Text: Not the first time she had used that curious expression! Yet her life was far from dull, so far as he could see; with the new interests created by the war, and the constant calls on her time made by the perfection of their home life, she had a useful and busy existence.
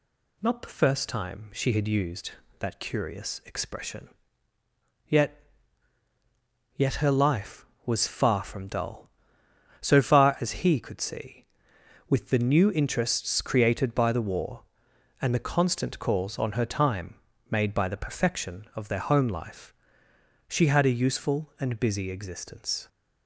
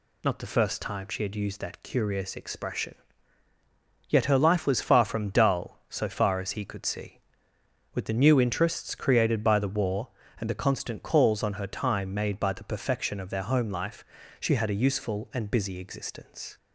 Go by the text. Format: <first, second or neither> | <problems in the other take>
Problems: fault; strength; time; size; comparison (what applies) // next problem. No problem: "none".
second | says "Yet" twice; at 6.7 s // pauses between "time" and "made"; slight; at 17.1 s; 0.34 s long